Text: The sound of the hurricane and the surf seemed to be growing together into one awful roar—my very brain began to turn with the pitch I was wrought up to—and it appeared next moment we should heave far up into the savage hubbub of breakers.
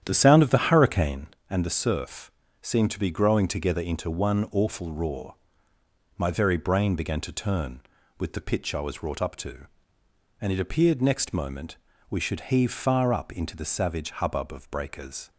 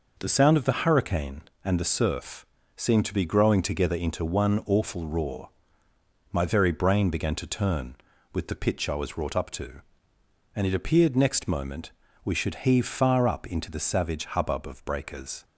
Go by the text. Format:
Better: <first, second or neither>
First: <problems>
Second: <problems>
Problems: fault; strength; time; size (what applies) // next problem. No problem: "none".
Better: second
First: starts louder than the rest; strong; until 1.4 s; 9.5 dB // pauses between "surf" and "seemed"; slight; at 2.2 s; 0.32 s long // pauses between "moment" and "we"; slight; at 11.7 s; 0.32 s long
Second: pauses between "surf" and "seemed"; slight; at 2.4 s; 0.32 s long // pauses between "moment" and "we"; slight; at 11.9 s; 0.32 s long